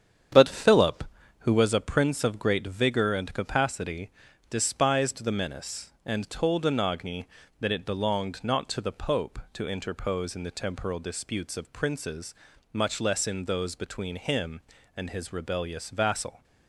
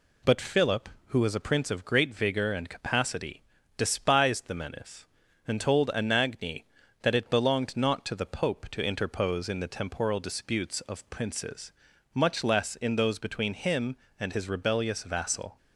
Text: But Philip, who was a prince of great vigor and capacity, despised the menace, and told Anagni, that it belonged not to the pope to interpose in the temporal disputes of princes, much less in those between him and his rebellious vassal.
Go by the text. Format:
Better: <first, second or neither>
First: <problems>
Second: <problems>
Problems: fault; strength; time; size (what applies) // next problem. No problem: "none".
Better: second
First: starts louder than the rest; strong; until 1.7 s; 8.5 dB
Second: none